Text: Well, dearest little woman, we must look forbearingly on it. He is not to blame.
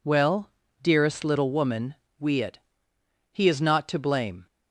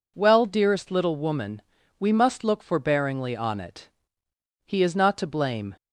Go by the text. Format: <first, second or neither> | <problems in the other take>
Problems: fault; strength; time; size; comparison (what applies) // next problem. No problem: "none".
second | skips "must look forbearingly on"; at 2.4 s